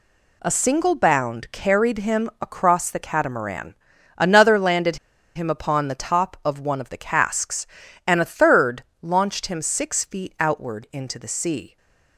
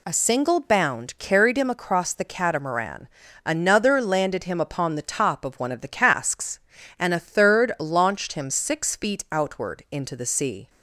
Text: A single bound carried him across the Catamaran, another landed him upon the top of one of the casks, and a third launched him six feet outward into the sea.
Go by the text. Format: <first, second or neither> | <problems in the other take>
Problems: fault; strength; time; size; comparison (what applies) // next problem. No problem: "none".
second | pauses between "landed" and "him"; at 4.9 s; 0.38 s long // pauses between "third" and "launched"; slight; at 8.8 s; 0.18 s long // stays silent after the last word; slight; from 11.6 s on; 0.5 s long